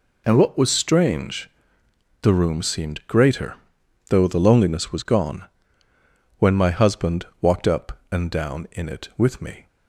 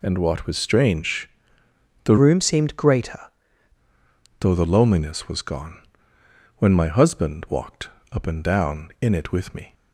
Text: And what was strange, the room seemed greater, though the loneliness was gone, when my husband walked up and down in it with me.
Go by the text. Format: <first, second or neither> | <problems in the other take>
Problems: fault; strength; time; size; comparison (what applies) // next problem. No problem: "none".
first | changes voice from "room" to "greater"; from 2.1 to 3.1 s; 1.0 s long // pauses between "walked" and "up"; slight; at 7.8 s; 0.24 s long